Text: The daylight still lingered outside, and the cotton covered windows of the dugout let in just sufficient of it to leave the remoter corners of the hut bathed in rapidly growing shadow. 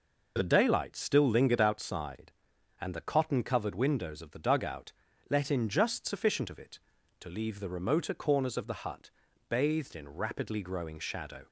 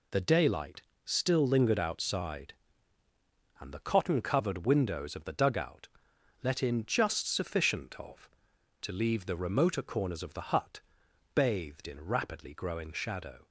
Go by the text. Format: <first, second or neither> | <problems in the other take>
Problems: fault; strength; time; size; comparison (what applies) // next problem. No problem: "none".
first | pauses between "daylight" and "still"; slight; at 0.8 s; 0.22 s long // pauses between "dugout" and "let"; noticeable; at 5.8 s; 0.54 s long; also in the first // skips "it"; at 8.5 s // pauses between "hut" and "bathed"; noticeable; at 10.7 s; 0.54 s long; also in the first